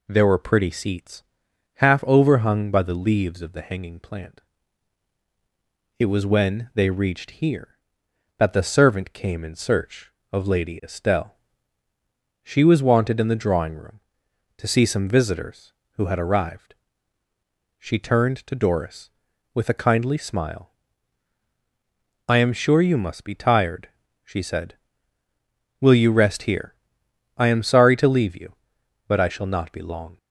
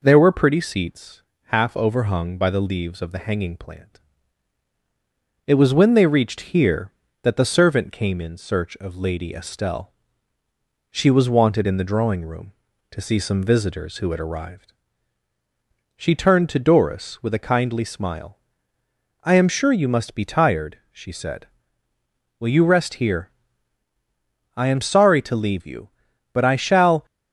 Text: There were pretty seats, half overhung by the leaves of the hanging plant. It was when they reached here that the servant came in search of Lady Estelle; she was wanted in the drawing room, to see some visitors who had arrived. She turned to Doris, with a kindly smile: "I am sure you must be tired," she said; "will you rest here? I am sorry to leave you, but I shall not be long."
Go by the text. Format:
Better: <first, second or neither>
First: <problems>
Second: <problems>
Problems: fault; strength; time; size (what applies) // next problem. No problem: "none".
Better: first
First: none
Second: stops before "not be long"; at 27.0 s